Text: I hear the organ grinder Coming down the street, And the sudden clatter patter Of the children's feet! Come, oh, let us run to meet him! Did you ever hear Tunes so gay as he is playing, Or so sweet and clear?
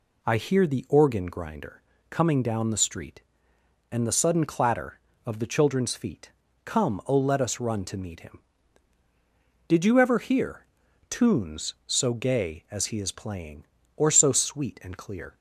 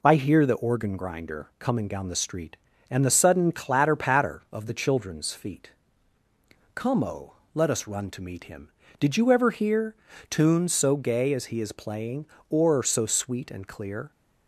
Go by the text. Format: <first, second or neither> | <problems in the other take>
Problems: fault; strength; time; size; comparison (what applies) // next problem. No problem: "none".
second | pauses between "grinder" and "Coming"; slight; at 1.8 s; 0.30 s long // skips "patter"; at 5.1 s // pauses between "hear" and "Tunes"; at 10.6 s; 0.44 s long; slight in the second